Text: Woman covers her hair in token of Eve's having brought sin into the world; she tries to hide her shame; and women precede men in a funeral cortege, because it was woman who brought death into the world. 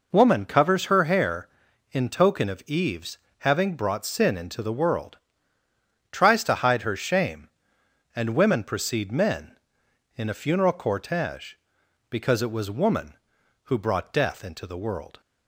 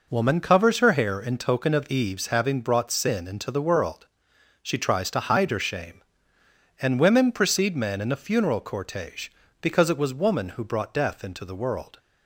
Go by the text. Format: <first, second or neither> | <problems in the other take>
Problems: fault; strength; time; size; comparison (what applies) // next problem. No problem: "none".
second | pauses between "Eve's" and "having"; slight; at 3.1 s; 0.22 s long // skips "she"; at 5.6 s